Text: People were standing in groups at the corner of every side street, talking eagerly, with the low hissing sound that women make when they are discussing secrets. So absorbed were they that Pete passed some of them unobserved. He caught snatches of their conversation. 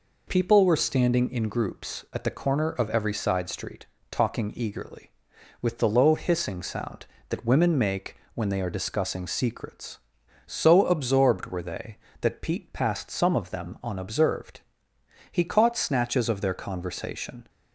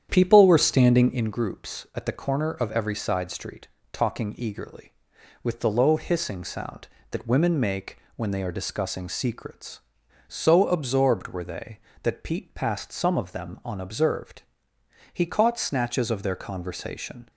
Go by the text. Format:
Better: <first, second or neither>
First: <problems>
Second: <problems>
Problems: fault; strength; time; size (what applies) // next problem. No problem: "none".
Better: first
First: pauses between "make" and "when"; slight; at 8.1 s; 0.20 s long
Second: starts louder than the rest; strong; until 1.3 s; 9.5 dB // pauses between "make" and "when"; slight; at 7.9 s; 0.20 s long